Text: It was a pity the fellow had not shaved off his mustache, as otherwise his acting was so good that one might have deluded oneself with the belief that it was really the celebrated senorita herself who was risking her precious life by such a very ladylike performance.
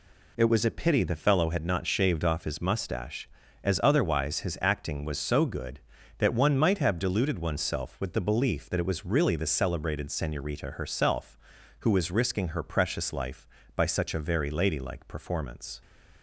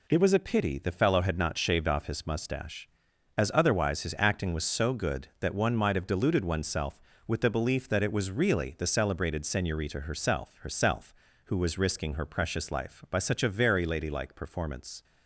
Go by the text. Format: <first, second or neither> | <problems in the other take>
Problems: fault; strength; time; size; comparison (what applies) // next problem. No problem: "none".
first | says "herself" twice; at 10.6 s